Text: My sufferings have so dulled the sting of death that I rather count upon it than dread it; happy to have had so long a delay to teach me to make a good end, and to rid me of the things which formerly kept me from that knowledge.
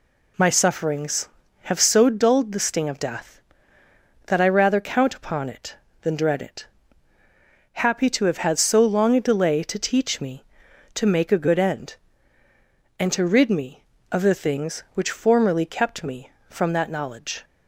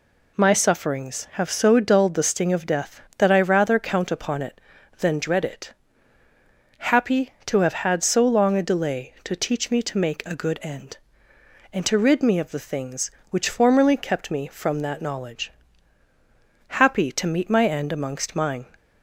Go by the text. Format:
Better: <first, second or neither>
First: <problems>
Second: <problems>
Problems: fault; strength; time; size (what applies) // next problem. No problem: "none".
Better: first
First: none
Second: goes on to say "Happy to meet my end amongst mine"; strong; from 16.6 s on; 1.9 s long